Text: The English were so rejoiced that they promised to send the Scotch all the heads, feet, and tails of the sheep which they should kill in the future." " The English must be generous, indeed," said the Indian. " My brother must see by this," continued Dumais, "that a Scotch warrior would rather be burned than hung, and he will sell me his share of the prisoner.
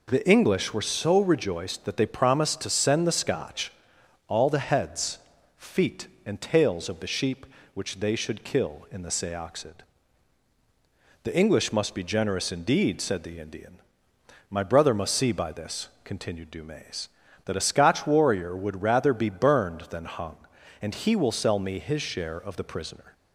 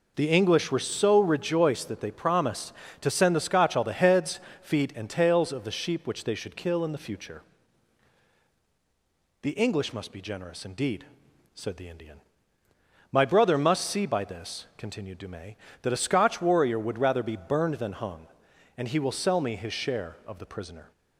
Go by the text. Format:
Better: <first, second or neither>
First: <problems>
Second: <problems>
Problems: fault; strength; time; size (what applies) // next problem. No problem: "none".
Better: second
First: pauses between "Scotch" and "all"; noticeable; at 3.7 s; 0.56 s long // says "seoxid" for "future"; at 9.1 s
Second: none